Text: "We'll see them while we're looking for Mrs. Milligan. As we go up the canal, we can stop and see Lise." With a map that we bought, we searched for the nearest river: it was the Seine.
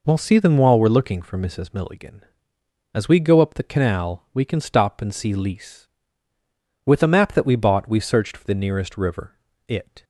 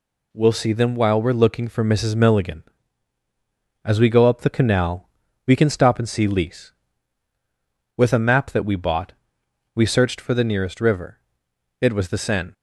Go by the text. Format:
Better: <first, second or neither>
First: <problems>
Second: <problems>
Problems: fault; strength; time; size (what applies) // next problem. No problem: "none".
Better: second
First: stops before "was the Seine"; at 10.0 s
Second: none